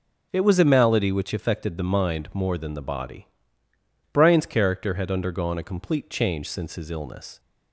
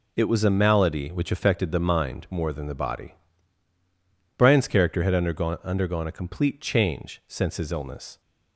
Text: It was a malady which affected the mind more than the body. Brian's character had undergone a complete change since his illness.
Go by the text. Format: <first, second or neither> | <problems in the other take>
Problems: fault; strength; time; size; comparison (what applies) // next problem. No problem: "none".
first | says "undergone" twice; at 5.6 s